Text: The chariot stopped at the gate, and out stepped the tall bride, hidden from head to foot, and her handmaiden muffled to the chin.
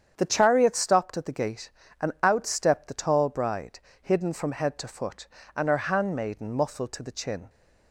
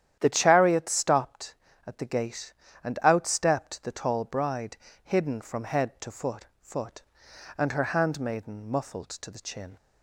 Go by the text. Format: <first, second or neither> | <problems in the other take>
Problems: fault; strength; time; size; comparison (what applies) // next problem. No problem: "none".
first | starts louder than the rest; strong; until 1.2 s; 10.5 dB; strong in the first // says "foot" twice; at 6.6 s